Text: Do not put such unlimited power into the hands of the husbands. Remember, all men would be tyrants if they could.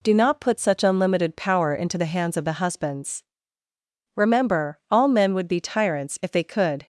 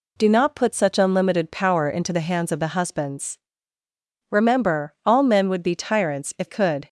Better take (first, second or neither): first